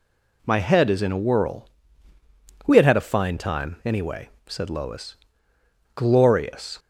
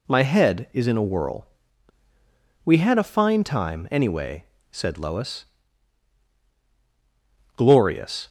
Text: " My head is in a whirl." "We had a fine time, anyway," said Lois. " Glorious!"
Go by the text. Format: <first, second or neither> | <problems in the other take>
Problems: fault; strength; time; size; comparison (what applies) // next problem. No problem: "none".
second | says "had" twice; at 2.8 s